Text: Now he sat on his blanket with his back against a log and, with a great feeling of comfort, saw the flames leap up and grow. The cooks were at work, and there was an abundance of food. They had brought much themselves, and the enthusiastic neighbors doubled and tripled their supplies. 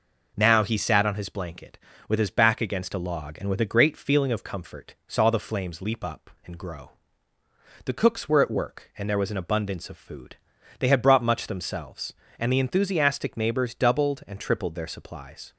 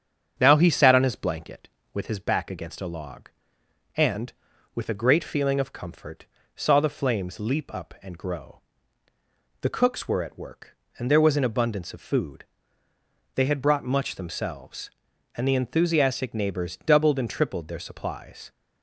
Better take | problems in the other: first | starts louder than the rest; strong; until 1.8 s; 7.5 dB

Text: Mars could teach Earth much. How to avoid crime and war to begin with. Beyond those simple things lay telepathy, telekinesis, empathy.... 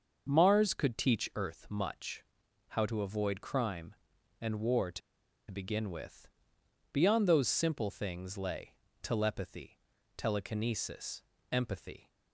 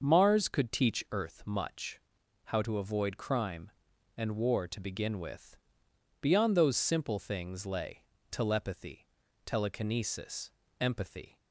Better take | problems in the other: second | starts louder than the rest; until 1.3 s; 6.5 dB; also in the second // pauses between "to" and "begin"; noticeable; at 5.0 s; 0.50 s long // pauses between "lay" and "telepathy"; slight; at 8.7 s; 0.28 s long; slight in the second

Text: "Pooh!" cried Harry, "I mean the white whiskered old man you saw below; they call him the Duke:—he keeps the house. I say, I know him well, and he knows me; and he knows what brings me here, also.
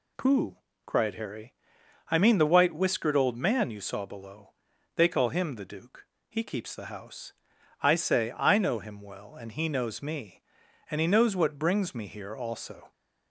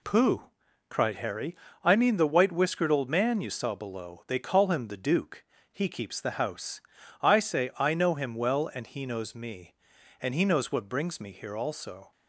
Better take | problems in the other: neither | none

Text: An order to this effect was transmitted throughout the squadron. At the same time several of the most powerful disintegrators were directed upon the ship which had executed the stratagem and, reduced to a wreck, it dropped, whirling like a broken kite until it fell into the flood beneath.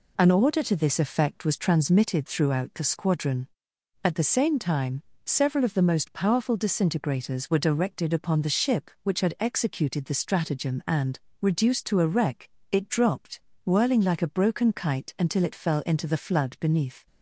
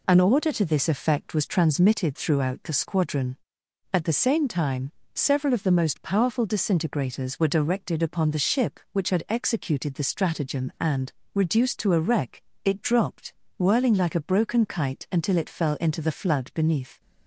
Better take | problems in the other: neither | pauses between "time" and "several"; slight; the same in both

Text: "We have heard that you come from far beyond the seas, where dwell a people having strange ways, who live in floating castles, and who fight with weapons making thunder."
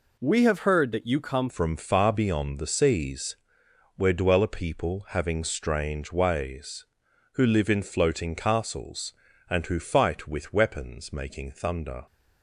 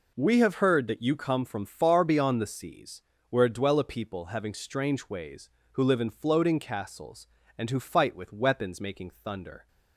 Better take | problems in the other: second | changes voice at "from"; from 1.4 s on; 10.6 s long

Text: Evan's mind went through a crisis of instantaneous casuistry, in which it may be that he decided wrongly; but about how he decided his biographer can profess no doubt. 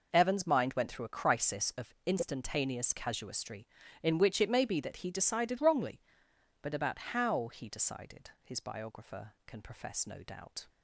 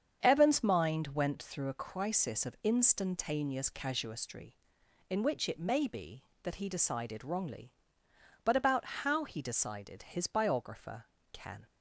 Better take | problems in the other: first | starts louder than the rest; strong; until 1.3 s; 7.5 dB // stops before "profess no doubt"; at 11.6 s

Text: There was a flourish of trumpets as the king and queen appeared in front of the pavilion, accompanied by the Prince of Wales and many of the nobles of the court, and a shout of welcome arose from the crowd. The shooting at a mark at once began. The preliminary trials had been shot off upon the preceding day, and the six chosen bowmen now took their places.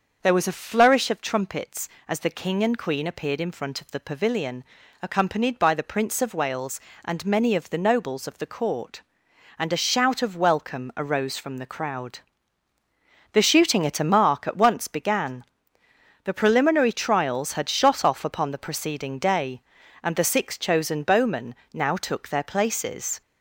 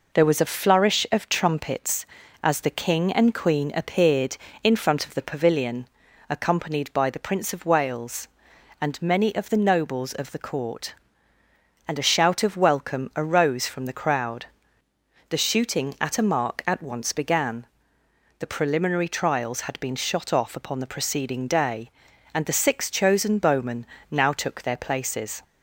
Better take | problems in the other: second | starts louder than the rest; until 1.2 s; 6.5 dB // skips "been"; at 17.6 s // pauses between "bowmen" and "now"; slight; at 21.5 s; 0.18 s long; slight in the second

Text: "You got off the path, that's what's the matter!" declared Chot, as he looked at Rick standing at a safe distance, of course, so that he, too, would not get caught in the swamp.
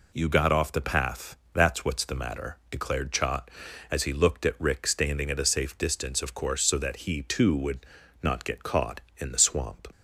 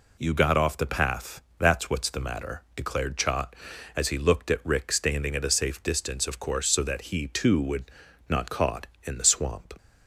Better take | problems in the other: first | pauses between "would" and "not"; slight; at 7.9 s; 0.36 s long; slight in the first // skips "get"; at 8.5 s

